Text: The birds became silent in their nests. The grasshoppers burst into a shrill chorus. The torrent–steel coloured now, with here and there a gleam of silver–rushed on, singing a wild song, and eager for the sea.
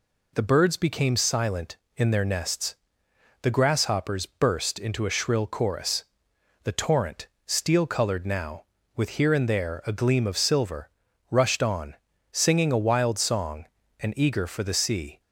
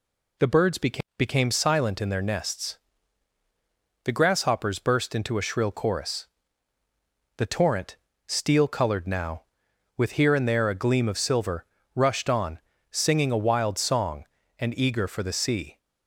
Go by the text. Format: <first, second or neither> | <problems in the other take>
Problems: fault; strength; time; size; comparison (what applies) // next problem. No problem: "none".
first | says "became" twice; at 1.1 s